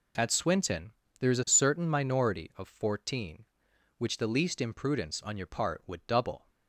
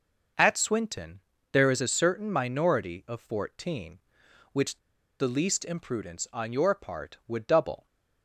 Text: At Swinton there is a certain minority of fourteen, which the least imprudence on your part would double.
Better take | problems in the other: first | pauses between "Swinton" and "there"; slight; at 1.2 s; 0.32 s long; slight in the first // pauses between "which" and "the"; at 4.7 s; 0.41 s long

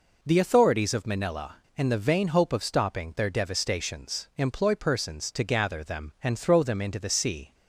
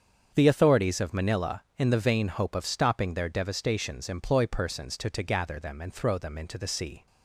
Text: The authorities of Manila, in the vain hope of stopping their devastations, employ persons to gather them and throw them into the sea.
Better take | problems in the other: first | starts louder than the rest; strong; until 1.3 s; 7.5 dB // says "to" twice; at 5.0 s

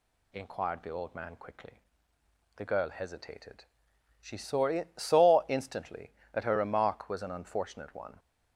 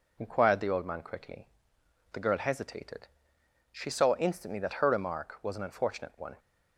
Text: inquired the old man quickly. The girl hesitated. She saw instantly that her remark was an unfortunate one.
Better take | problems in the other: second | says "saw" twice; at 4.9 s

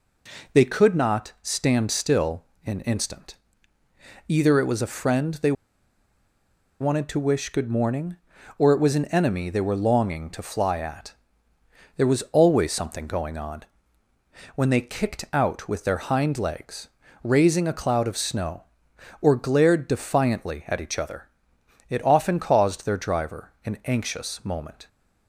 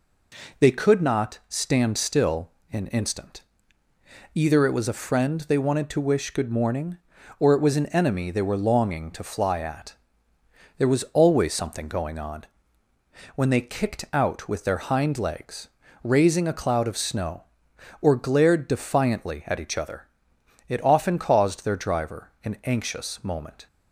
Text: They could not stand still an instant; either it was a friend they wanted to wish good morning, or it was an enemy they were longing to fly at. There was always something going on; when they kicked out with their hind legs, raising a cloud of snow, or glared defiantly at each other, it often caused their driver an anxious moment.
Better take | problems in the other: second | pauses between "still" and "an"; slight; at 2.4 s; 0.20 s long; slight in the second // pauses between "they" and "wanted"; strong; at 5.5 s; 1.2 s long

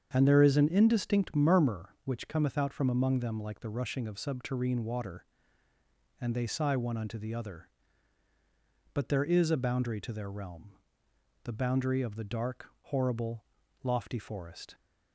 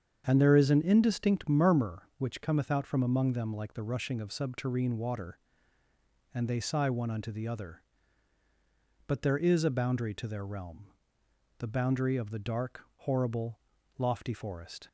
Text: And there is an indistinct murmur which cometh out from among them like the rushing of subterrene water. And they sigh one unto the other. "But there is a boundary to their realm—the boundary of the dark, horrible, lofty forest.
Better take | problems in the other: neither | starts louder than the rest; strong; the same in both

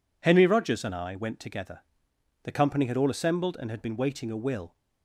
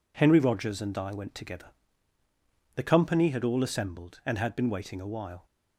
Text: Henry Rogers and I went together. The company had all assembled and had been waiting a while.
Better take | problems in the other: second | says "will" for "while"; at 4.3 s

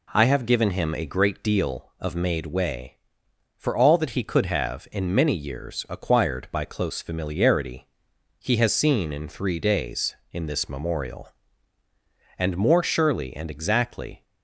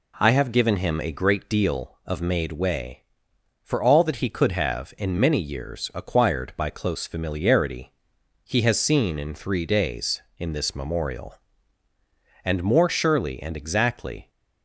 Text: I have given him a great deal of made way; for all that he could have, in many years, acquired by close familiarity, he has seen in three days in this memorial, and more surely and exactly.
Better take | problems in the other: neither | none

